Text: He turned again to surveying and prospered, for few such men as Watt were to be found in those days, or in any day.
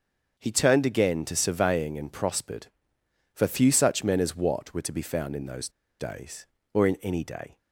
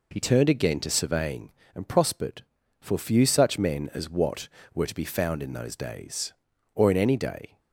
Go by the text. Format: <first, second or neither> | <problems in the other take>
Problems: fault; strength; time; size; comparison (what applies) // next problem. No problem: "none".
second | starts louder than the rest; until 1.4 s; 6.5 dB // pauses between "those" and "days"; slight; at 5.6 s; 0.30 s long